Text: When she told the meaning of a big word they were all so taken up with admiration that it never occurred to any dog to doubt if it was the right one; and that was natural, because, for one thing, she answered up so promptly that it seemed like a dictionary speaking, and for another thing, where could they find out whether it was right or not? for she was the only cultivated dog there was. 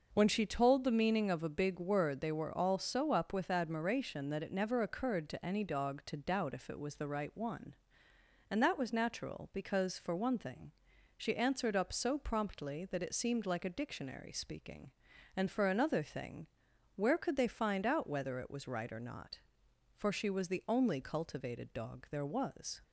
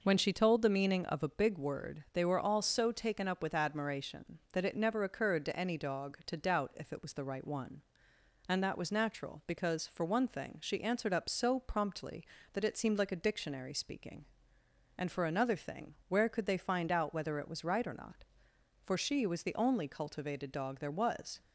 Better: second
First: skips "taken"; at 3.1 s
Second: none

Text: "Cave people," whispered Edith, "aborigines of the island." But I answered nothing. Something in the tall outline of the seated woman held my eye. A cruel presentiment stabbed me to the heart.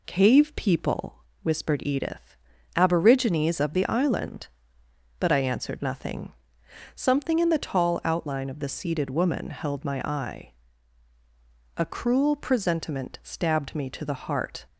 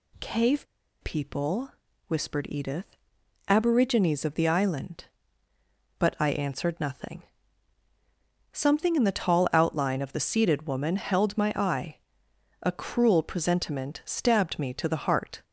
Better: first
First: none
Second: pauses between "Cave" and "people"; at 0.6 s; 0.37 s long

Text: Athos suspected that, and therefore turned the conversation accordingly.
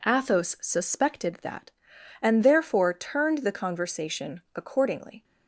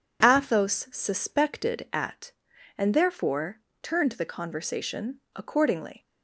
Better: first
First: none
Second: says "at" for "that"; at 1.9 s // pauses between "therefore" and "turned"; slight; at 3.5 s; 0.22 s long // pauses between "conversation" and "accordingly"; slight; at 5.1 s; 0.16 s long

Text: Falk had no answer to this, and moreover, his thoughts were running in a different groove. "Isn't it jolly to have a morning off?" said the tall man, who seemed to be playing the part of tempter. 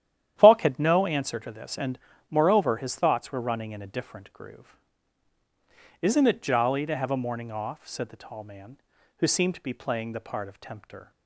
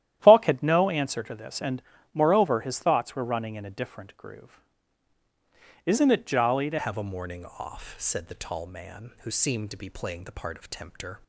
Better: first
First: starts louder than the rest; strong; until 1.3 s; 11 dB // pauses between "and" and "moreover"; slight; at 1.9 s; 0.32 s long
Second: starts louder than the rest; strong; until 1.2 s; 12 dB // pauses between "and" and "moreover"; slight; at 1.8 s; 0.32 s long // changes voice at "have"; from 6.7 s on; 4.5 s long

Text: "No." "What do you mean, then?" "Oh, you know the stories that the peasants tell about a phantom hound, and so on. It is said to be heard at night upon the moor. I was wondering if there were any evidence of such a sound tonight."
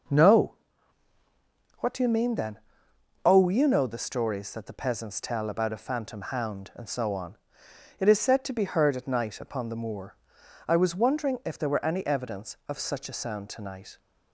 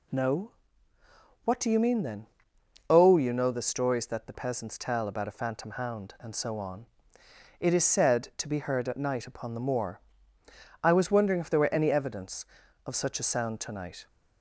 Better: neither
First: none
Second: none

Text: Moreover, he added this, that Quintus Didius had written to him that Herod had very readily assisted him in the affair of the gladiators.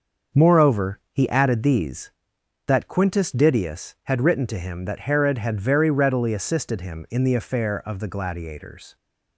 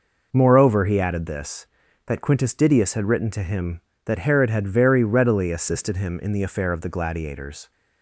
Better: second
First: starts louder than the rest; until 1.4 s; 6.5 dB // says "these" for "this"; at 1.6 s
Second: none

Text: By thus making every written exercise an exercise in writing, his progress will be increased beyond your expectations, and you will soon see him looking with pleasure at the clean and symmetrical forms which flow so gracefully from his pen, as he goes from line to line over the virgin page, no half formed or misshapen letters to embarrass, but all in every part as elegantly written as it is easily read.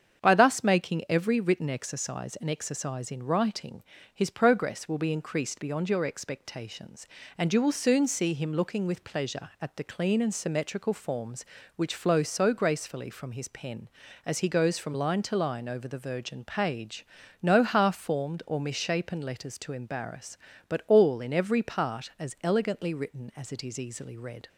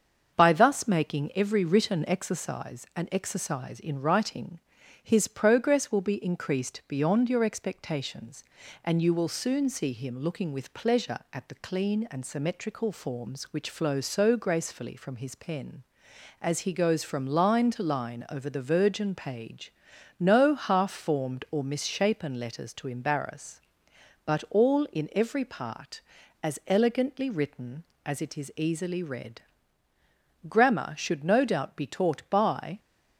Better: first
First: starts louder than the rest; strong; until 1.2 s; 7.5 dB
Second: starts louder than the rest; until 1.4 s; 7 dB // goes on to say "Grammar should no doubt be taught by"; strong; from 30.4 s on; 2.3 s long

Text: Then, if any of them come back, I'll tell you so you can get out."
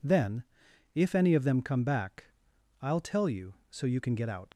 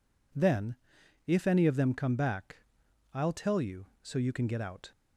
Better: second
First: leaves "out" unfinished; at 4.5 s; 70 ms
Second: none

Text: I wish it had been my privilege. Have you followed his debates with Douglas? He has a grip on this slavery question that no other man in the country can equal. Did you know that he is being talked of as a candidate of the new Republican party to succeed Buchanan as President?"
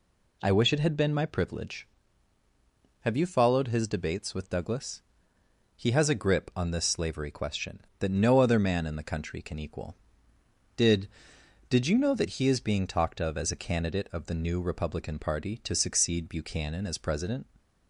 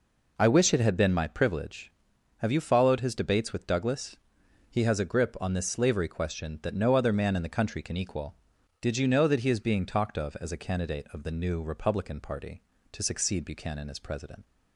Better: second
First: says "Did" twice; at 11.6 s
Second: none

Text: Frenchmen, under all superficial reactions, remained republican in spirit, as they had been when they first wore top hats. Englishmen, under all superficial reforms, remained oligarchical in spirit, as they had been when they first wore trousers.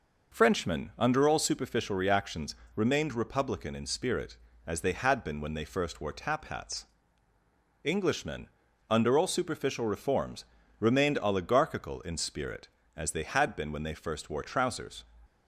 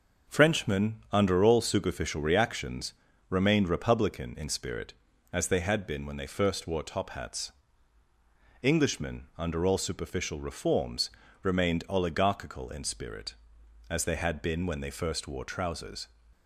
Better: second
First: says "tap" for "top"; at 6.1 s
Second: none

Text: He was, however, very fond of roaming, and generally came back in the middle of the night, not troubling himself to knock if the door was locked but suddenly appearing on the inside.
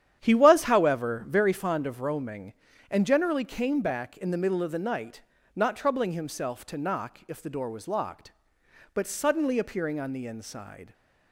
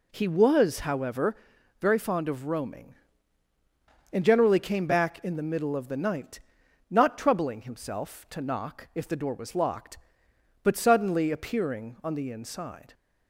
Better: second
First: starts louder than the rest; strong; until 1.5 s; 10 dB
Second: none

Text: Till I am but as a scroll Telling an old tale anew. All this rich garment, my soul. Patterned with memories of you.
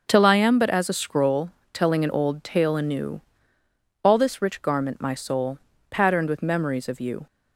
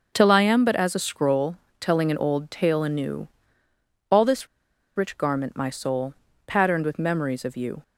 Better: first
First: starts louder than the rest; until 1.0 s; 6 dB // pauses between "scroll" and "Telling"; slight; at 1.4 s; 0.22 s long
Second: starts louder than the rest; until 1.1 s; 6 dB // pauses between "scroll" and "Telling"; slight; at 1.5 s; 0.24 s long // pauses between "this" and "rich"; noticeable; at 4.4 s; 0.49 s long

